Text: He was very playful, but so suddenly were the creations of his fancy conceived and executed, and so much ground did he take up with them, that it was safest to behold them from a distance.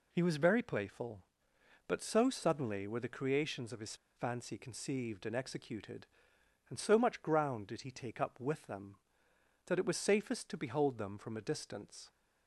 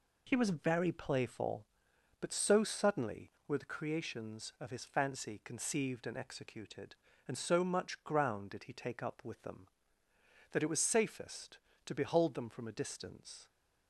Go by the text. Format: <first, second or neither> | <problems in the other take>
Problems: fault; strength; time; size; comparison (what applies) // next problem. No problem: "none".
second | pauses between "his" and "fancy"; slight; at 3.9 s; 0.21 s long